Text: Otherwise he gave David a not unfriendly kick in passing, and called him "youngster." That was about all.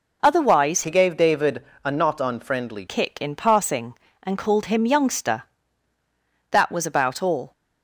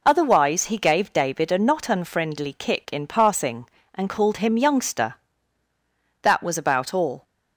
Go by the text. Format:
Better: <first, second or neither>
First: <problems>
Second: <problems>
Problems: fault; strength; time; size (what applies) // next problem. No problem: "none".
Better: second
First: changes voice from "he" to "unfriendly"; from 0.8 to 2.8 s; 2.0 s long // pauses between "David" and "a"; slight; at 1.6 s; 0.20 s long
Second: none